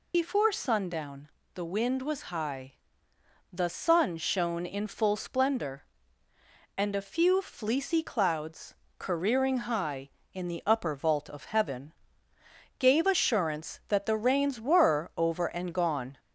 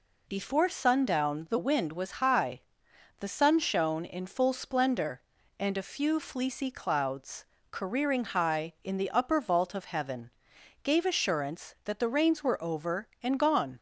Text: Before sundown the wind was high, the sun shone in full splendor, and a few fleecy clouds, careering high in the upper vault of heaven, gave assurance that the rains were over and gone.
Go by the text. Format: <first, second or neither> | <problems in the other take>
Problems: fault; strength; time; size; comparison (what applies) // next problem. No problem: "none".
second | loses the start of "Before"; at 0.1 s; 75 ms // pauses between "sundown" and "the"; slight; at 1.2 s; 0.26 s long